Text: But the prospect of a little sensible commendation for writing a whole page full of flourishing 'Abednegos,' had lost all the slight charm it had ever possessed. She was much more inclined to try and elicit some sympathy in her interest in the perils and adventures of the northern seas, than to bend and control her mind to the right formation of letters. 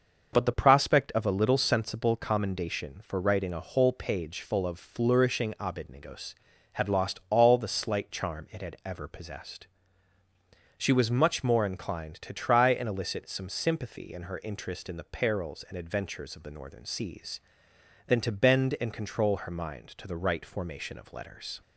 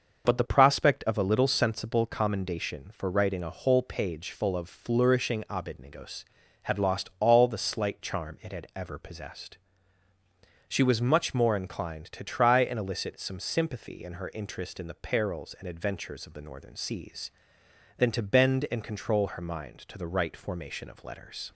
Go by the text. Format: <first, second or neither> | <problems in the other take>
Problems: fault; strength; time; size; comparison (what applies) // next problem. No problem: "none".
neither | starts louder than the rest; the same in both